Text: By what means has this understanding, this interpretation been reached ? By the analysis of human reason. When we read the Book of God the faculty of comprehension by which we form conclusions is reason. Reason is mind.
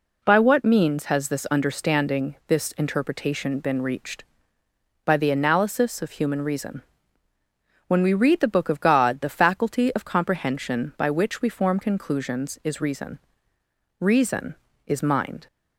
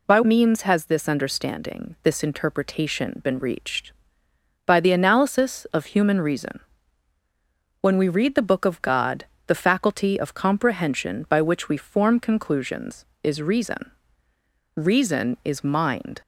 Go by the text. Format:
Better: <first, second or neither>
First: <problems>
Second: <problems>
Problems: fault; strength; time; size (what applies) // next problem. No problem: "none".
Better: first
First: none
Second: skips "what"; at 0.2 s // pauses between "God" and "the"; slight; at 9.2 s; 0.22 s long